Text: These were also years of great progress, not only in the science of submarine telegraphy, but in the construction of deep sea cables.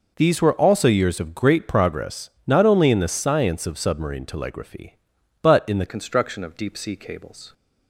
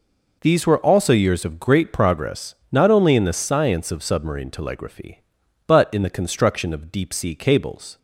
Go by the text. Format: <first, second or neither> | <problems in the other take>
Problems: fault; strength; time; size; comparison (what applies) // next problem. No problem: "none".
second | changes voice at "construction"; from 5.8 s on; 1.7 s long